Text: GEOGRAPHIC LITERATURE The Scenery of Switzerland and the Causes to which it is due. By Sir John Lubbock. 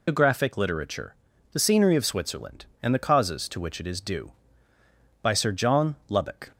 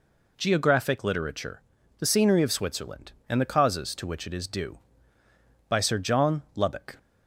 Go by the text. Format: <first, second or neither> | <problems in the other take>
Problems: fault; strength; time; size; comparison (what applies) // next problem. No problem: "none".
second | loses the start of "GEOGRAPHIC"; at 0.0 s; 175 ms // pauses between "LITERATURE" and "The"; at 1.1 s; 0.38 s long; also in the second